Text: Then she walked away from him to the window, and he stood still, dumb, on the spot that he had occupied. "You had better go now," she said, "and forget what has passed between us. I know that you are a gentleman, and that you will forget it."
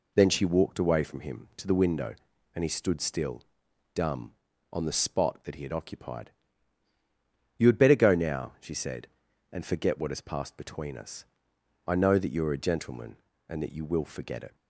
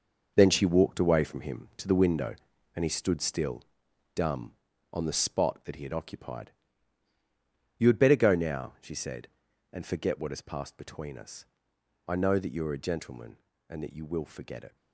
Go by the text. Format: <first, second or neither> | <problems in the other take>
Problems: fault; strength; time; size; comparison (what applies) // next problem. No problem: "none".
first | gets quieter; strong; throughout; 10 dB